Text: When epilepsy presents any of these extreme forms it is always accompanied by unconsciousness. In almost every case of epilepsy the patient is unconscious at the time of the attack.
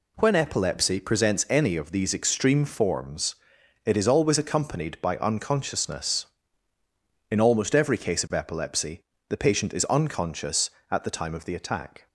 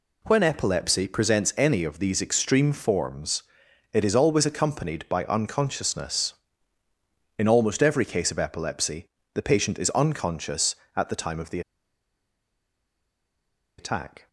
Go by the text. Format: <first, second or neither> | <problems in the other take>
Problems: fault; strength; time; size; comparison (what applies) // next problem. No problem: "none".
first | pauses between "forms" and "it"; noticeable; at 3.4 s; 0.50 s long; noticeable in the first // pauses between "epilepsy" and "the"; slight; at 9.0 s; 0.28 s long; slight in the first // pauses between "the" and "attack"; strong; at 11.6 s; 2.1 s long